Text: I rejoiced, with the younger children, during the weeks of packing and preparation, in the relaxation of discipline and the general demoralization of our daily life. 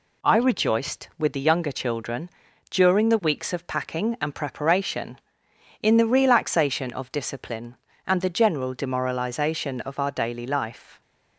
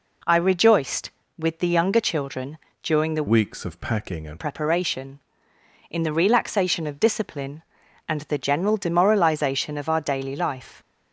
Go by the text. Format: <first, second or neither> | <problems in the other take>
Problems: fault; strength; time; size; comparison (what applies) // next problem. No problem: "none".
first | changes voice from "weeks" to "and"; from 3.2 to 4.3 s; 1.1 s long